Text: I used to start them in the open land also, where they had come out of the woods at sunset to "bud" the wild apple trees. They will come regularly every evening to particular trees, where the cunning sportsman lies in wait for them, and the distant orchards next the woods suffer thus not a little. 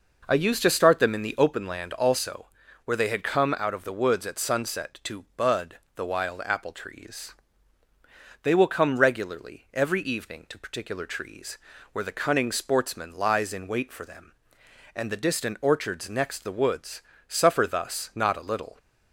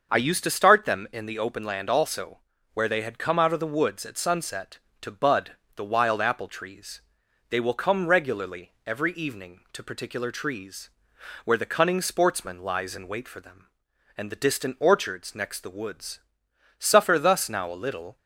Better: first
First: pauses between "bud" and "the"; slight; at 5.7 s; 0.16 s long // pauses between "woods" and "suffer"; slight; at 17.0 s; 0.26 s long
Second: starts louder than the rest; until 1.1 s; 6.5 dB // pauses between "bud" and "the"; slight; at 5.5 s; 0.20 s long // pauses between "woods" and "suffer"; noticeable; at 16.2 s; 0.58 s long // says "now" for "not"; at 17.4 s

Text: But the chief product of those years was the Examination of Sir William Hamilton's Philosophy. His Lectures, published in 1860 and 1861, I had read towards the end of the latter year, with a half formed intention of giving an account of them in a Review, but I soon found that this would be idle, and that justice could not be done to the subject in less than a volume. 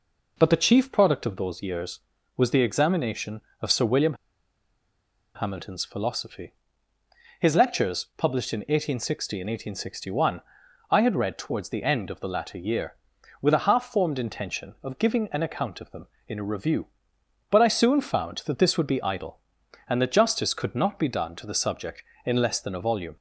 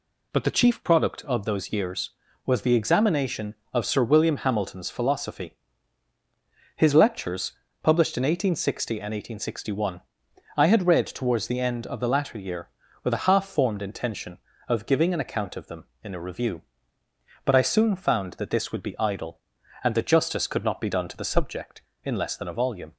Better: second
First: pauses between "William" and "Hamilton's"; at 4.1 s; 1.2 s long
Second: none

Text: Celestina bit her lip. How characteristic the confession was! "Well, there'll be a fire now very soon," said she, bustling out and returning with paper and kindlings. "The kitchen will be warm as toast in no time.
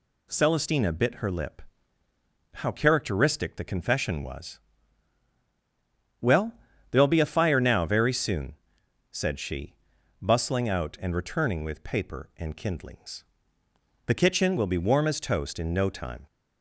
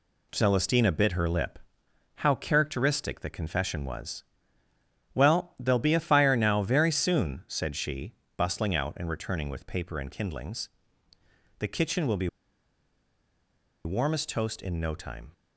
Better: first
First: none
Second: pauses between "be" and "warm"; strong; at 12.2 s; 1.5 s long

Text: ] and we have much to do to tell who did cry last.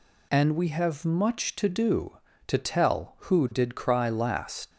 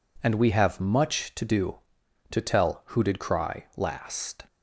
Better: second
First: leaves "last" unfinished; at 4.7 s; 75 ms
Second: none

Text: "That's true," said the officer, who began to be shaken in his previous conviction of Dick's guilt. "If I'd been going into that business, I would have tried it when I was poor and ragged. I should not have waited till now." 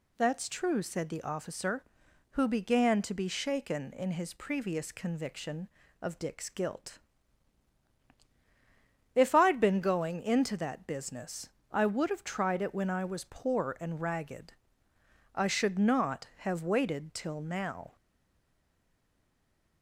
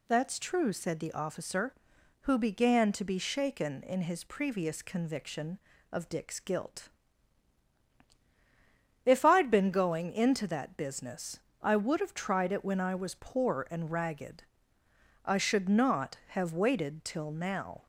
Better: second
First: stays silent after the last word; noticeable; from 17.9 s on; 1.9 s long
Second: none

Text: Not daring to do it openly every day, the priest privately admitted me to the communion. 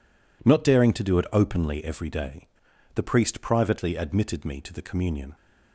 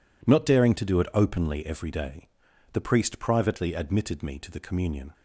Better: neither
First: none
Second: none

